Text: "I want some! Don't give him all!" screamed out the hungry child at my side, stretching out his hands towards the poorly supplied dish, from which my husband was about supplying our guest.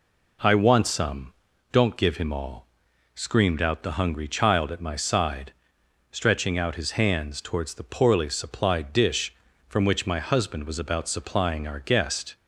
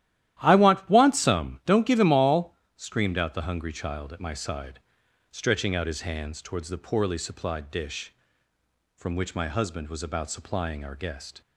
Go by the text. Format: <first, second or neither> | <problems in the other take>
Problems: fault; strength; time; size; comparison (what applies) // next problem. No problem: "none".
first | starts louder than the rest; strong; until 1.4 s; 13 dB // says "want" twice; at 0.8 s